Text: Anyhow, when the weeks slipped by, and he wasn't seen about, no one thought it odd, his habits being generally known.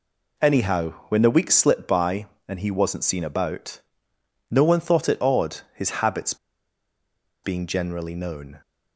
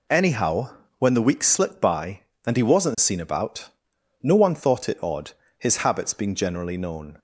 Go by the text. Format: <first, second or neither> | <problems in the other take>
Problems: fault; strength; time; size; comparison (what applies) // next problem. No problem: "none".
second | pauses between "habits" and "being"; at 6.3 s; 1.0 s long